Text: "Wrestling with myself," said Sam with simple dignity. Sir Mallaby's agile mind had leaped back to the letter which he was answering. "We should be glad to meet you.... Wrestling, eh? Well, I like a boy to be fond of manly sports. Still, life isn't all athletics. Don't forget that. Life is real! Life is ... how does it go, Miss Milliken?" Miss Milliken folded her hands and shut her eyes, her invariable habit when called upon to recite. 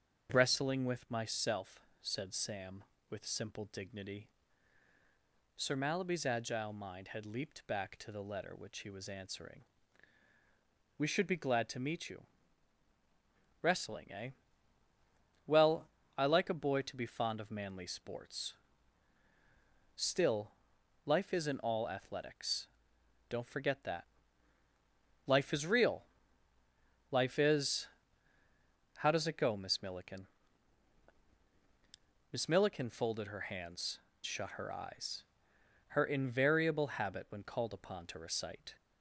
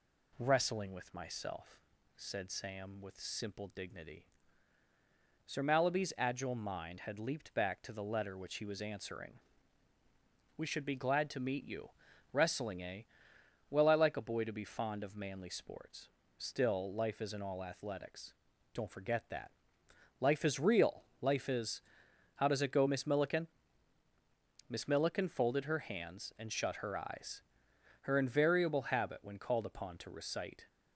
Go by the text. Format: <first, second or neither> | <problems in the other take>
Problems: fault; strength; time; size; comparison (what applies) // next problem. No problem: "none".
second | starts louder than the rest; strong; until 1.3 s; 7.5 dB // skips "and"; at 34.1 s